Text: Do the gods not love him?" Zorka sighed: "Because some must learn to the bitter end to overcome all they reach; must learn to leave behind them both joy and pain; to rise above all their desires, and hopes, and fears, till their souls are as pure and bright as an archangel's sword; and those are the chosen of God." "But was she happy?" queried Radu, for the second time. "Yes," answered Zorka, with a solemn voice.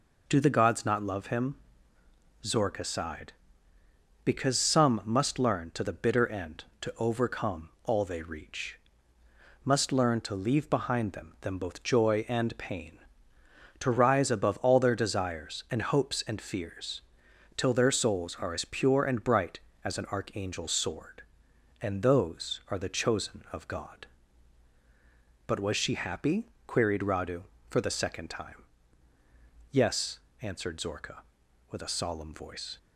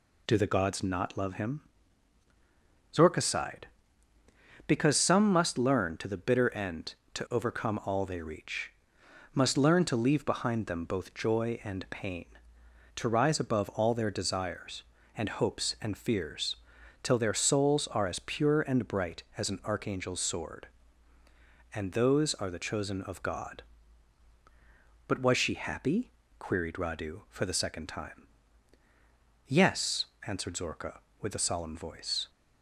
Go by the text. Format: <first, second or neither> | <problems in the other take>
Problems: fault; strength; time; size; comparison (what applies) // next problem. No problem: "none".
second | pauses between "overcome" and "all"; slight; at 7.6 s; 0.16 s long // says "them" twice; at 11.4 s